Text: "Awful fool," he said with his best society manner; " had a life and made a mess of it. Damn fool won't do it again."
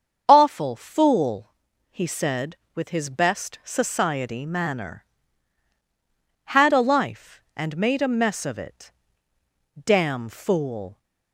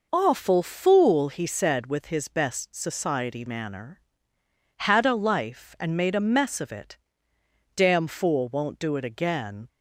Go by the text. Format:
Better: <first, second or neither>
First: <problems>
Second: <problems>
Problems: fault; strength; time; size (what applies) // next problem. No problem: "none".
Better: second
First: starts louder than the rest; strong; until 1.2 s; 7.5 dB // stops before "won't do it again"; at 10.9 s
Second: none